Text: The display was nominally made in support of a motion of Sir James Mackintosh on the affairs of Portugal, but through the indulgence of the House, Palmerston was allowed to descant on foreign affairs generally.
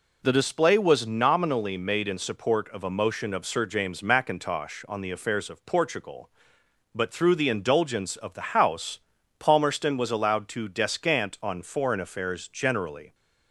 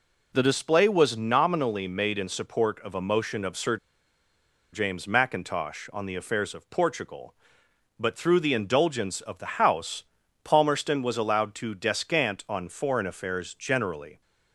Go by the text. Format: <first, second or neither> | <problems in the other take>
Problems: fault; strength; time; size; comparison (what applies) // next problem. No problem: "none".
first | pauses between "Sir" and "James"; noticeable; at 3.7 s; 0.95 s long